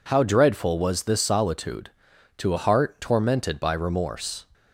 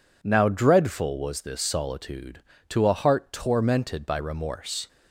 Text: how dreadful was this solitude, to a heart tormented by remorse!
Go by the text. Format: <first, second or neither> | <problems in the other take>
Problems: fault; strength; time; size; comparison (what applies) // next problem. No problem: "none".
first | says "now" for "how"; at 0.2 s